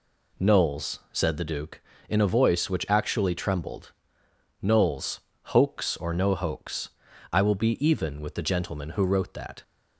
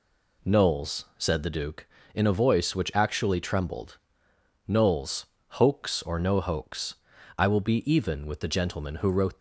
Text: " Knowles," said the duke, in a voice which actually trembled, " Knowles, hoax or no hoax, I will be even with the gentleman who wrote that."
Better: first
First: none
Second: stops before "that"; at 9.3 s

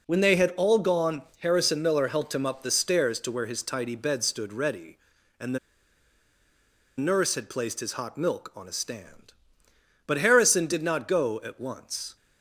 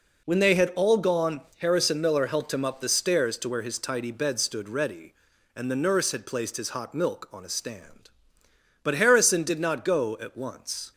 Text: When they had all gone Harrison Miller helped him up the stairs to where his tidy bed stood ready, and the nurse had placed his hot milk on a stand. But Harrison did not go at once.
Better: second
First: pauses between "gone" and "Harrison"; slight; at 1.2 s; 0.18 s long // pauses between "the" and "nurse"; strong; at 5.5 s; 1.4 s long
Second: pauses between "gone" and "Harrison"; slight; at 1.4 s; 0.18 s long

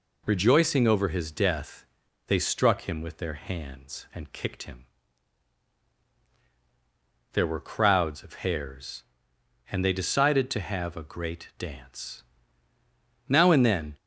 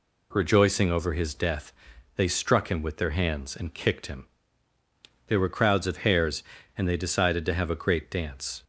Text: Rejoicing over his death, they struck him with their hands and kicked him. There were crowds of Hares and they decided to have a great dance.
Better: second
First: goes on to say "Now and then"; noticeable; from 13.2 s on; 0.68 s long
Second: none

